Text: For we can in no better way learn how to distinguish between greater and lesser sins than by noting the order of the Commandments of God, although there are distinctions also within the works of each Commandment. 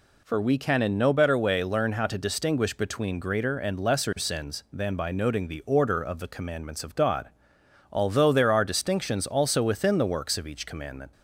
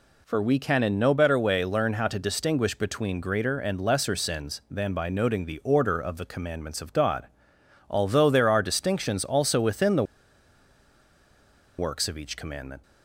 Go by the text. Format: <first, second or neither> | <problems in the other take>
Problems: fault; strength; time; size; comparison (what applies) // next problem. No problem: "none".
first | pauses between "the" and "works"; strong; at 10.0 s; 1.7 s long